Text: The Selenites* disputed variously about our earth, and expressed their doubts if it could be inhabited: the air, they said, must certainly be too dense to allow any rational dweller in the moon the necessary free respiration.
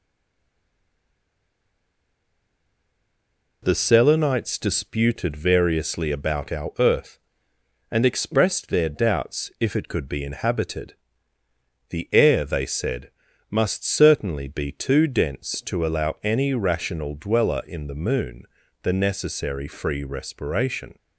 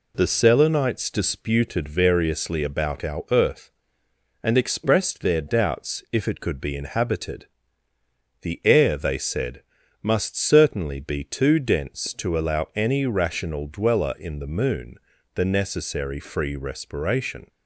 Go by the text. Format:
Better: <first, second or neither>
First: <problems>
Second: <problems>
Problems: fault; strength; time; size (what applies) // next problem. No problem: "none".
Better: second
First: stays silent before the first word; strong; until 3.6 s; 3.6 s long // pauses between "moon" and "the"; at 18.4 s; 0.38 s long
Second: pauses between "moon" and "the"; at 14.9 s; 0.38 s long